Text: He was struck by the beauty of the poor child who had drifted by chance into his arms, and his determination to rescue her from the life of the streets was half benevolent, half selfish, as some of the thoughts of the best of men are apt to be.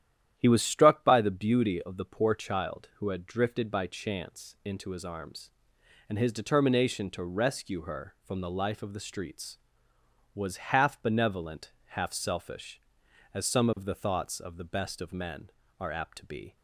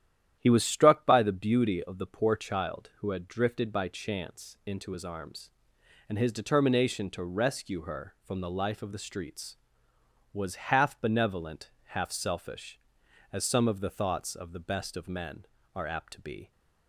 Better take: neither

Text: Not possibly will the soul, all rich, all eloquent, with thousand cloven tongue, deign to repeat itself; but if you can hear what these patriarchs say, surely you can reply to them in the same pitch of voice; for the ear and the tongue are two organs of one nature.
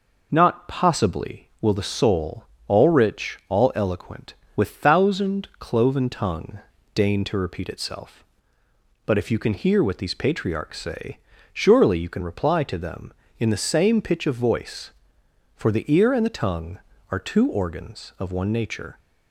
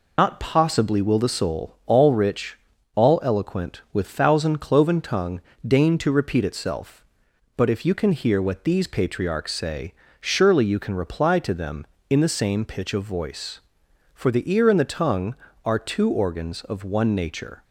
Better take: first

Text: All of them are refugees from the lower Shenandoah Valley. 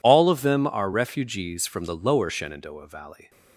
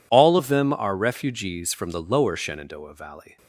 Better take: neither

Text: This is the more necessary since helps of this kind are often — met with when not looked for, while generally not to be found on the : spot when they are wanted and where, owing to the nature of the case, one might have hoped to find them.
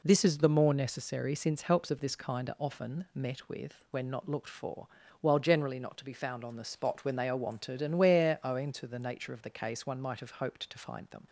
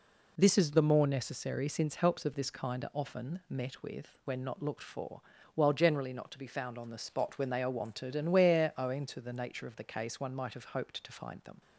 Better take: neither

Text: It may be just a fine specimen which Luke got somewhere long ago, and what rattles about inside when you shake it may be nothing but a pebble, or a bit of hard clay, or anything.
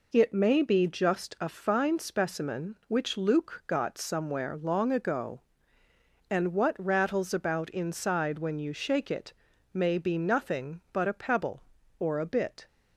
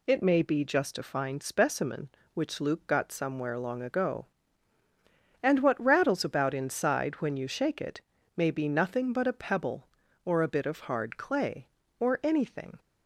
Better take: second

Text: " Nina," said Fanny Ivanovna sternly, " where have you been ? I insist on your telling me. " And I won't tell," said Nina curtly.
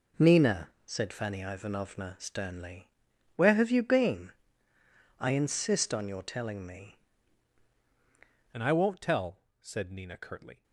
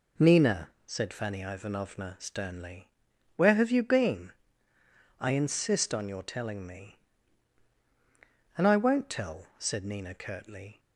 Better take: second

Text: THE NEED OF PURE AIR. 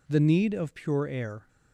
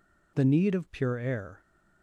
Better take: neither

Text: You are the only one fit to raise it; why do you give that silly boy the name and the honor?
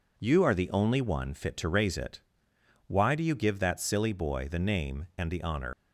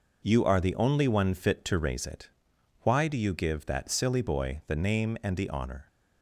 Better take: second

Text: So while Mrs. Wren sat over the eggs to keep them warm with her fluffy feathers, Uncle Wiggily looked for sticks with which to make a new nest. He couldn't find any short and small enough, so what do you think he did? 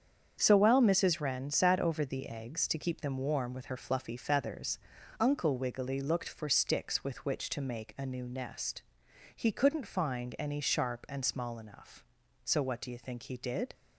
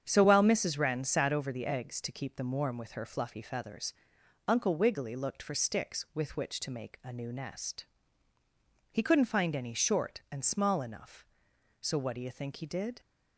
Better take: second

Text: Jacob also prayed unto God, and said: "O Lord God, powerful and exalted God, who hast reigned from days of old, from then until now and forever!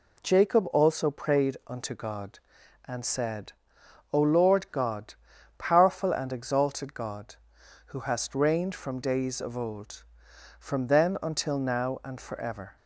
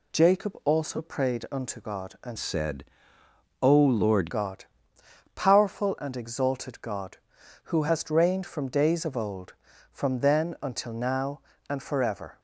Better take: first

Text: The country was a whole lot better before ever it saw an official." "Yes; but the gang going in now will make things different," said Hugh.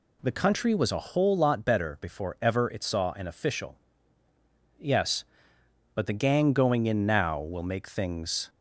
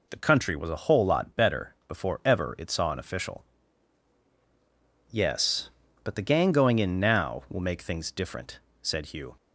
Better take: second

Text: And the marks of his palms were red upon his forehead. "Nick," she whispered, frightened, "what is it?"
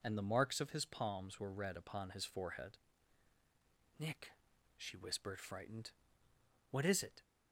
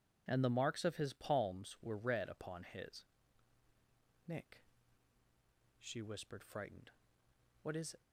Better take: first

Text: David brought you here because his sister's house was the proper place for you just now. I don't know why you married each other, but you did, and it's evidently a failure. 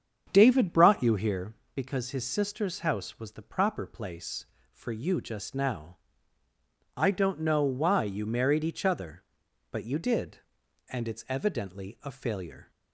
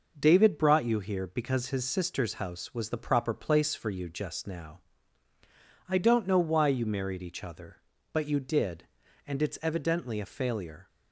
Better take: second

